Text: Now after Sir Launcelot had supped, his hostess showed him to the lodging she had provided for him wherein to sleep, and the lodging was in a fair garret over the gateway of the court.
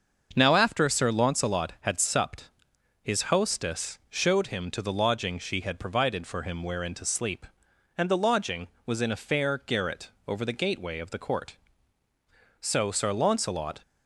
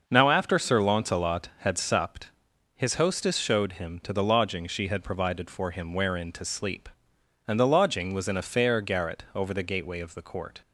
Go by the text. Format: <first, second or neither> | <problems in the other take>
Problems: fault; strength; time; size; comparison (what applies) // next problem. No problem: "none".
second | starts louder than the rest; until 1.3 s; 6.5 dB; noticeable in the second // pauses between "garret" and "over"; slight; at 10.0 s; 0.16 s long // goes on to say "So Sir Launcelot"; noticeable; from 12.5 s on; 1.2 s long